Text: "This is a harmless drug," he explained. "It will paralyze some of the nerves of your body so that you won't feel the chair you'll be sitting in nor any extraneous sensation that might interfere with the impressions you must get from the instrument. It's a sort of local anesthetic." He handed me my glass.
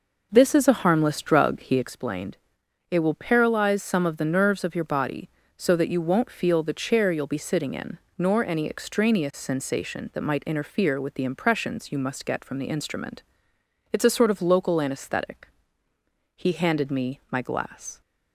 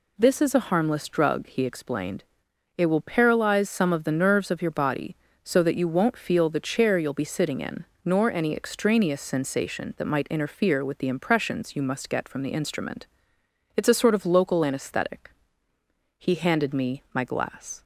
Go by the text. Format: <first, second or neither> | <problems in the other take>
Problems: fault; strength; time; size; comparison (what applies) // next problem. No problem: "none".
second | starts louder than the rest; noticeable; until 2.0 s; 5.5 dB // pauses between "in" and "nor"; slight; at 7.9 s; 0.18 s long; slight in the second